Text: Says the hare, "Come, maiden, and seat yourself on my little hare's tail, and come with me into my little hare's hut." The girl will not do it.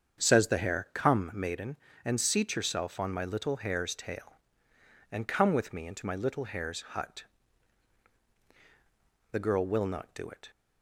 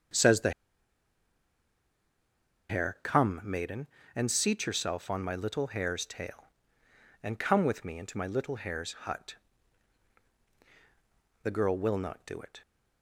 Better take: first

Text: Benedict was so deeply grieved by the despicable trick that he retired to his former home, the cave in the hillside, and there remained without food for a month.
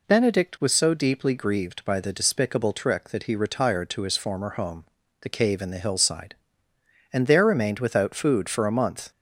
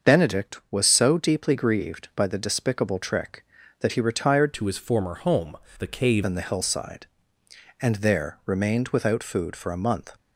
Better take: first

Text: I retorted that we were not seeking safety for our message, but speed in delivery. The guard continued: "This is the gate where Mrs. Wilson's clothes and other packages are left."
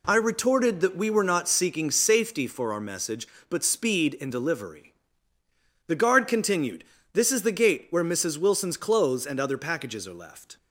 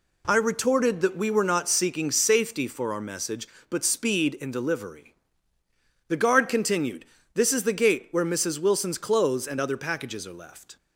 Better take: neither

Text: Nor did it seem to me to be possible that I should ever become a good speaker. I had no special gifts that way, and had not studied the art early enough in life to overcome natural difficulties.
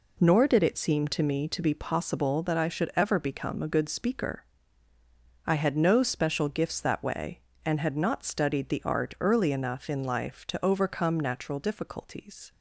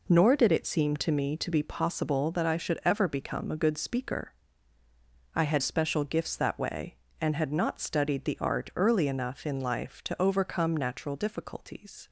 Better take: first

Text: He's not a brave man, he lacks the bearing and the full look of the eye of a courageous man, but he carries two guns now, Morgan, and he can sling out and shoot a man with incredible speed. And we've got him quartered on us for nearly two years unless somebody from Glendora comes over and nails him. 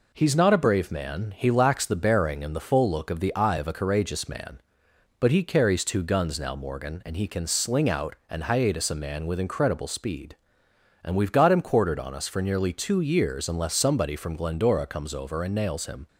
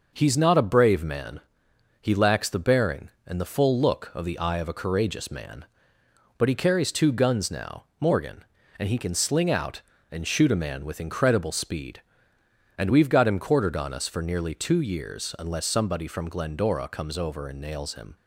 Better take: second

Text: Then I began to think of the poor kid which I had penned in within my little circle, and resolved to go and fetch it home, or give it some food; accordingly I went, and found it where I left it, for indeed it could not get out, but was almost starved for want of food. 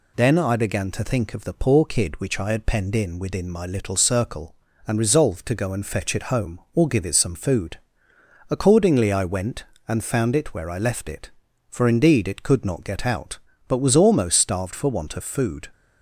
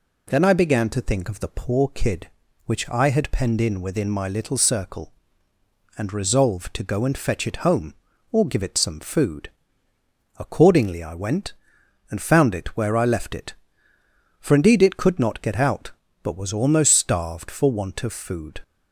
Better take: neither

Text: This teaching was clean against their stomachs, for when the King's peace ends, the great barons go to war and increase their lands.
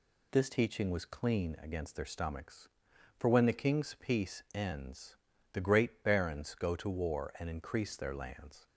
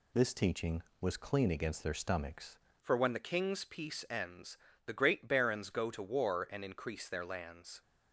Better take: first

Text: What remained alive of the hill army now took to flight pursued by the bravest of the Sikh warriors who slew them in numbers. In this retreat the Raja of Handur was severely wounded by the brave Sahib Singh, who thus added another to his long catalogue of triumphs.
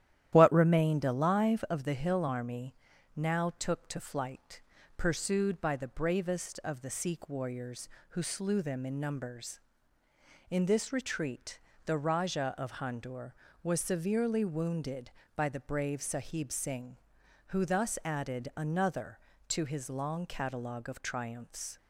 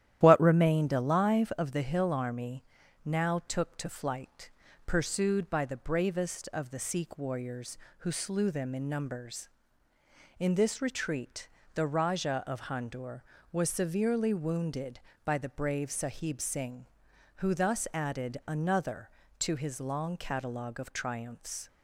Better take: neither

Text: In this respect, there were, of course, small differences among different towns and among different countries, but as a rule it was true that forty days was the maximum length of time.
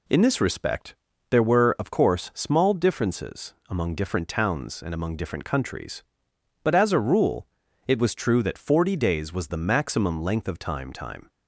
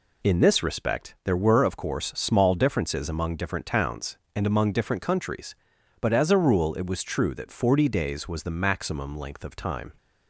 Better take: second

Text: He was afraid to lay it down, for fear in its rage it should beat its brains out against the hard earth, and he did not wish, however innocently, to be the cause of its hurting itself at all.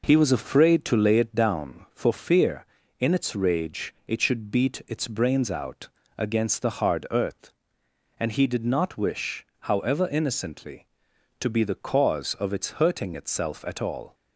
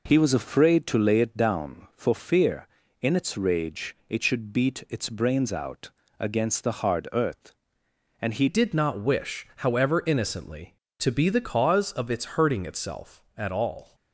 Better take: first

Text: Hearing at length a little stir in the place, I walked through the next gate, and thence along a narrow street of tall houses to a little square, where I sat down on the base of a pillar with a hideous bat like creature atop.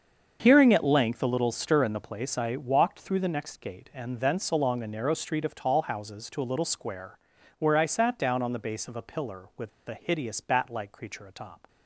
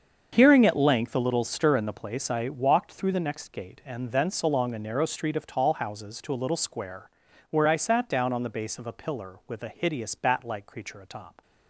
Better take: second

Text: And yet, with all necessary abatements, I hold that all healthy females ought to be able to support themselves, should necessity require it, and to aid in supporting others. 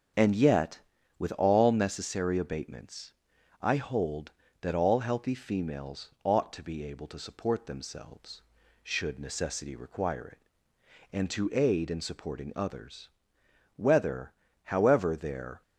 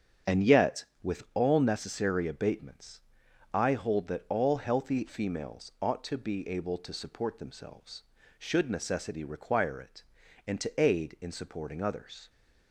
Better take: second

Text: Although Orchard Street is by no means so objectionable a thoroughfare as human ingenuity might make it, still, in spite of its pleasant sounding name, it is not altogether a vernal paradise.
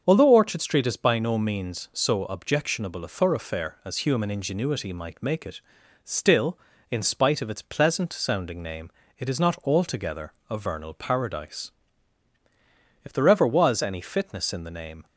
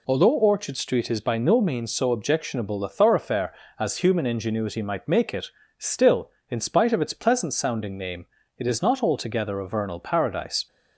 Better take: second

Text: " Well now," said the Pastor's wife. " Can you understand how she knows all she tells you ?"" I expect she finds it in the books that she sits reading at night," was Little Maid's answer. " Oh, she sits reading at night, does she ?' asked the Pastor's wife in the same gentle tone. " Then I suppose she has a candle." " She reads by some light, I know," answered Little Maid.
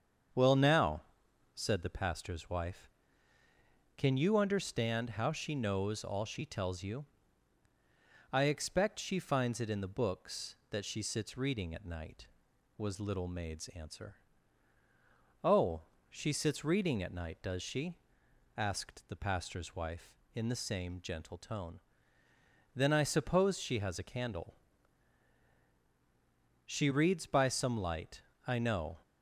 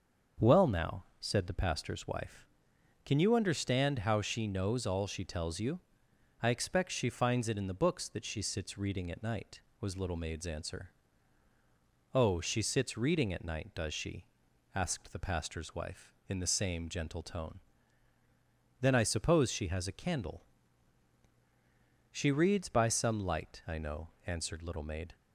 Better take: second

